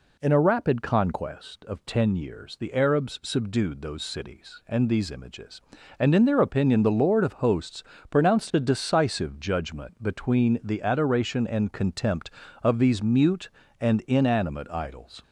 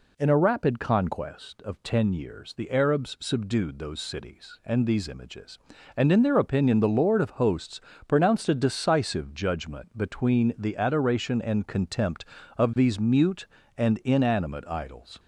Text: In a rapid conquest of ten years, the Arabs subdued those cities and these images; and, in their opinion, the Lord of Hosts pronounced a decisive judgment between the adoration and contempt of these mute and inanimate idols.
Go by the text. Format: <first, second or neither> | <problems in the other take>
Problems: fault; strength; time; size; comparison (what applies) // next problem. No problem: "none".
neither | pauses between "Hosts" and "pronounced"; slight; the same in both